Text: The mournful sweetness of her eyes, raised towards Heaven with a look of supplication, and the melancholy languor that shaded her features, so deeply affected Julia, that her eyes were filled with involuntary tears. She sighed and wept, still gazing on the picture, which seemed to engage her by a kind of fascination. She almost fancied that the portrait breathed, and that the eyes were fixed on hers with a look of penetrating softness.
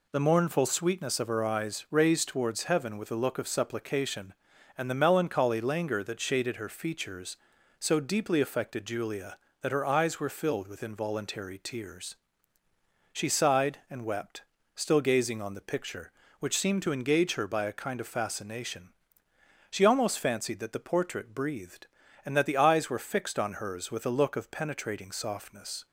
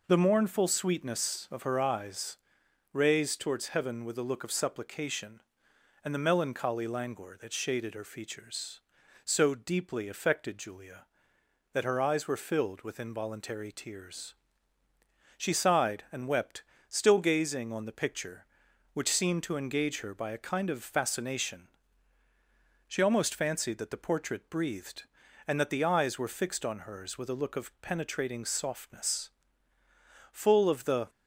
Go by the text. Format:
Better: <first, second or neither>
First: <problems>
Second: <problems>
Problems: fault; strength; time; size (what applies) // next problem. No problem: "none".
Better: first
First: none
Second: goes on to say "Full of the"; noticeable; from 30.3 s on; 0.78 s long